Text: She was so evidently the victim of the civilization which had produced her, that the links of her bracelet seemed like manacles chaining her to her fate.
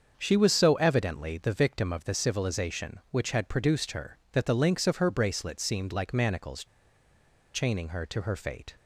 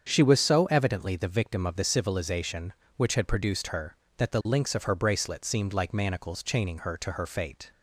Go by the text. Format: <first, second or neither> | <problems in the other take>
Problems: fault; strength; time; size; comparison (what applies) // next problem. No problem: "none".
second | starts louder than the rest; until 1.1 s; 7 dB; strong in the second // pauses between "manacles" and "chaining"; noticeable; at 6.6 s; 0.89 s long